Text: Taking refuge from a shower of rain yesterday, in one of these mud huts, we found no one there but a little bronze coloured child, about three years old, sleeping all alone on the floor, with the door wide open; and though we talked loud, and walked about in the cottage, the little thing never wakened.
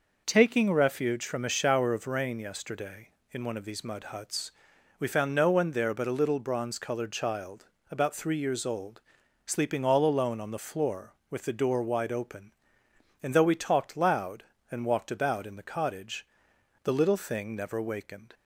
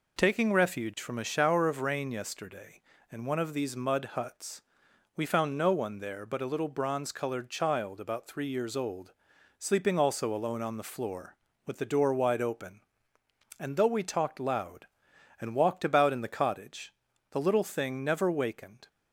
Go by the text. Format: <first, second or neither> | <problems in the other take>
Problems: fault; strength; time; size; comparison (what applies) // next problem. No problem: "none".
first | says "also" for "all"; at 9.9 s